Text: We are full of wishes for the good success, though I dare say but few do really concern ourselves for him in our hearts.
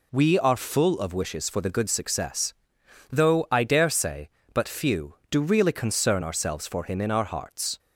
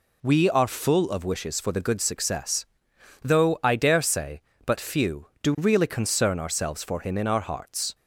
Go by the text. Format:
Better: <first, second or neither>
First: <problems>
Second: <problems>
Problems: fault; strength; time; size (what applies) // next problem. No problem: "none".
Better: neither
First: none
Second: none